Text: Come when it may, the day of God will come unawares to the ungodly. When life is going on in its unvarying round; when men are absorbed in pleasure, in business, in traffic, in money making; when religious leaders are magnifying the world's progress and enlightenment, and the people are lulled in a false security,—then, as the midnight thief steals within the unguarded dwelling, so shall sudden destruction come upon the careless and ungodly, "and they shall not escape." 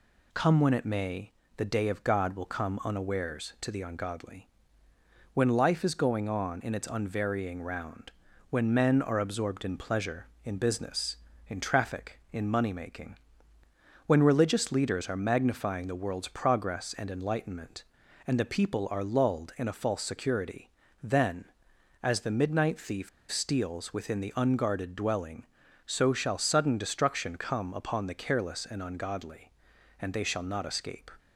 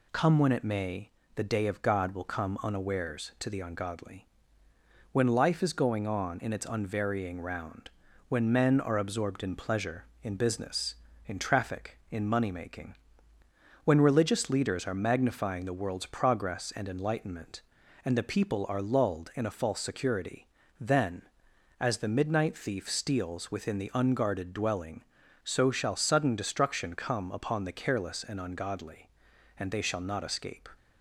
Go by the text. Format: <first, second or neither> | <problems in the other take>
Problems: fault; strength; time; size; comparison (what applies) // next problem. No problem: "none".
second | pauses between "thief" and "steals"; slight; at 23.0 s; 0.22 s long